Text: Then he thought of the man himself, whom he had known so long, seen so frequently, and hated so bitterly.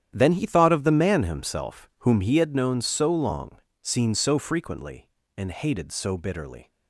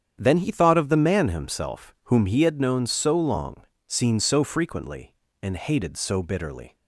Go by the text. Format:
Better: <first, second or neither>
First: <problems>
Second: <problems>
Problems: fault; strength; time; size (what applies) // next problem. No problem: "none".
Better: second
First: gets quieter; strong; throughout; 13.5 dB // starts louder than the rest; strong; until 1.1 s; 10 dB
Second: starts louder than the rest; strong; until 1.1 s; 8.5 dB